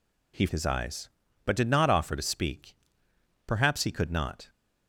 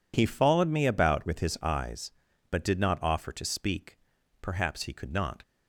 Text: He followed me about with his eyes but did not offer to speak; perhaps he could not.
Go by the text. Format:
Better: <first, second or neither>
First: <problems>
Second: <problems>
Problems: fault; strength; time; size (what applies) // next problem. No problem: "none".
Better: second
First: skips "followed me about with"; at 0.4 s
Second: none